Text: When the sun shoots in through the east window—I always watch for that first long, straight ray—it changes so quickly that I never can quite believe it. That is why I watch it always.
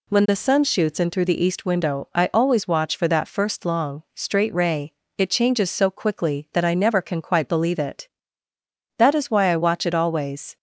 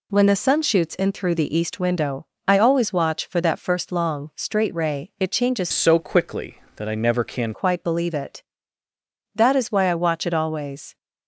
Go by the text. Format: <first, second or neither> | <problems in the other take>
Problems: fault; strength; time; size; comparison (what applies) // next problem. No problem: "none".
first | changes voice from "so" to "can"; from 5.7 to 7.5 s; 1.8 s long